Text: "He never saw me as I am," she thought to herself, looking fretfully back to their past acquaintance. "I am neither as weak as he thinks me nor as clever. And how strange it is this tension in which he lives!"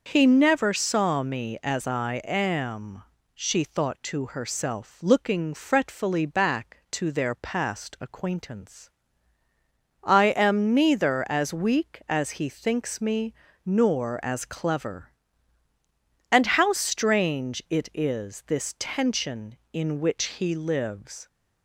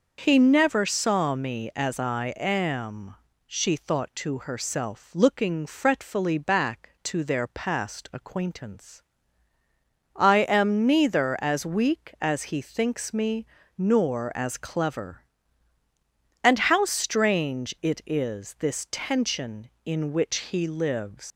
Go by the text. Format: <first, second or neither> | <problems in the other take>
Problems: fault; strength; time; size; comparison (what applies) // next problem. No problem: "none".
first | pauses between "me" and "nor"; slight; at 13.4 s; 0.32 s long; slight in the first // leaves "lives" unfinished; at 21.3 s; 90 ms